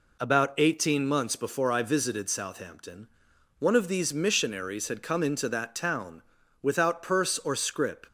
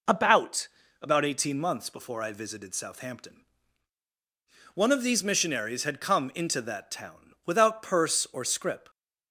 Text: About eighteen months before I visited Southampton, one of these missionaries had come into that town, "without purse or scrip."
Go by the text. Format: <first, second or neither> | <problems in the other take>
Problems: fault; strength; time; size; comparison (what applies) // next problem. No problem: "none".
first | says "About" twice; at 0.9 s